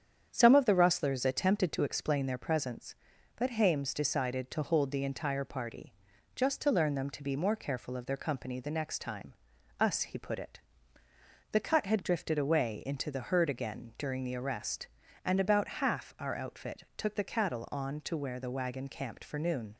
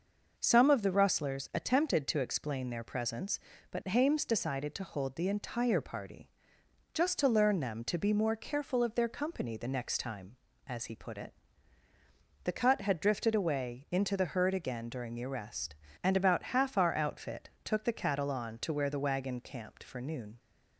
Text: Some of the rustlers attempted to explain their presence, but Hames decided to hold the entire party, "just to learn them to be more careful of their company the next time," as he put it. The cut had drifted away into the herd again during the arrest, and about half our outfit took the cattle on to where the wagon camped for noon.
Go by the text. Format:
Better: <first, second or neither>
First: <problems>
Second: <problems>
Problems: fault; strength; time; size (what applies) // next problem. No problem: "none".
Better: second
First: starts louder than the rest; strong; until 1.3 s; 8.5 dB // says "us" for "as"; at 9.7 s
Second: none